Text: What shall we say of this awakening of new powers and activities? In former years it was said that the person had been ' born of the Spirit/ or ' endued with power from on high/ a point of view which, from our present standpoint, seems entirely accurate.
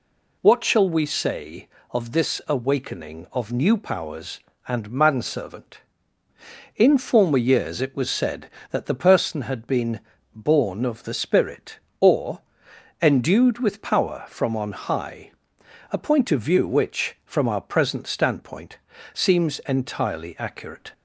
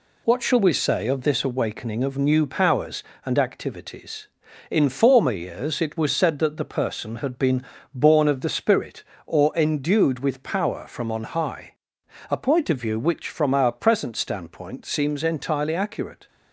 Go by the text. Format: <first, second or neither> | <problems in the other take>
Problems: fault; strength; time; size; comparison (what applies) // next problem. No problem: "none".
second | says "manservant" for "activities"; at 4.8 s